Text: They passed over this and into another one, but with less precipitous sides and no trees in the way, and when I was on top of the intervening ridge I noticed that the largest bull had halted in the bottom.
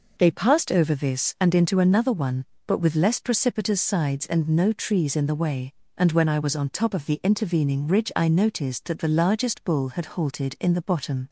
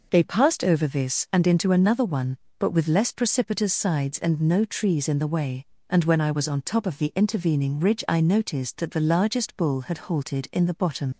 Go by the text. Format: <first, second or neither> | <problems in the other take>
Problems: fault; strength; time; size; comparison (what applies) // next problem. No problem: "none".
first | leaves "bottom" unfinished; at 11.1 s; 85 ms